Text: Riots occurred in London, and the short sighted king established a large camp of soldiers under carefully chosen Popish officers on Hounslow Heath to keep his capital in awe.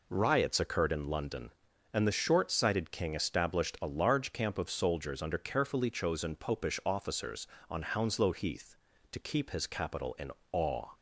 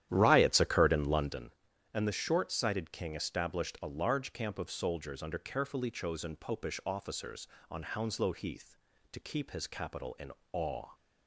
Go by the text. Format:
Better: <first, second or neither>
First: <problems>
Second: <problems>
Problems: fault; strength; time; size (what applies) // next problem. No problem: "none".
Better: first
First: pauses between "in" and "awe"; slight; at 10.3 s; 0.20 s long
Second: starts louder than the rest; strong; until 1.4 s; 11.5 dB // pauses between "in" and "awe"; slight; at 10.3 s; 0.20 s long